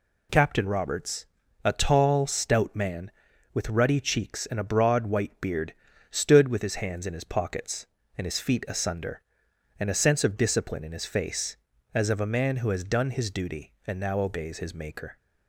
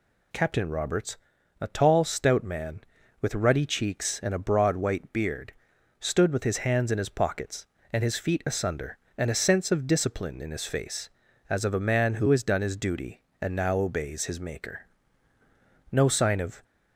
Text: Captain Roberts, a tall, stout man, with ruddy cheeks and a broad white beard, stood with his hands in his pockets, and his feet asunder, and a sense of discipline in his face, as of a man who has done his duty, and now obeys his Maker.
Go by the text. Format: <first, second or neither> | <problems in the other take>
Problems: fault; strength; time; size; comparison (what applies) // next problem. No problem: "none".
first | goes on to say "No sign of"; noticeable; from 15.9 s on; 0.72 s long